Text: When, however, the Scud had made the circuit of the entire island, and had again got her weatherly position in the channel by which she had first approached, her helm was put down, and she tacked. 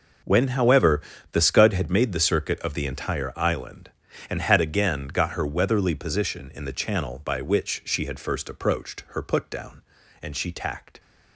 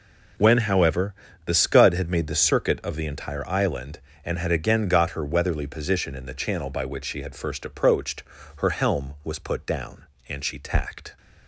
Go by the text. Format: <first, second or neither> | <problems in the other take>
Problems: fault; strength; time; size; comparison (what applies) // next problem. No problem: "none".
second | skips "helm was"; at 9.2 s